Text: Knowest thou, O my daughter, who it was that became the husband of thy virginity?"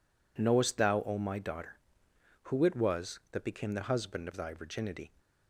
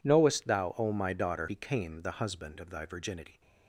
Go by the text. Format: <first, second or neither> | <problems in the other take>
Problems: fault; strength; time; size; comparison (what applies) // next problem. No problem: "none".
first | skips "who it was that"; at 1.4 s